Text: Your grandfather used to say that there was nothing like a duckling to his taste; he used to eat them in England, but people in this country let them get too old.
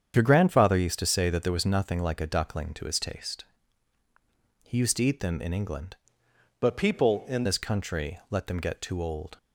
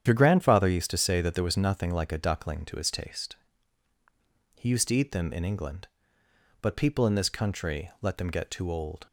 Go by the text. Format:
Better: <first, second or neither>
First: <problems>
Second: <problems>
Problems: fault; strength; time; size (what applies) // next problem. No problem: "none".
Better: second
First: starts louder than the rest; strong; until 1.1 s; 8 dB // changes voice from "but" to "in"; from 6.5 to 7.4 s; 0.9 s long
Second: starts louder than the rest; strong; until 1.0 s; 9 dB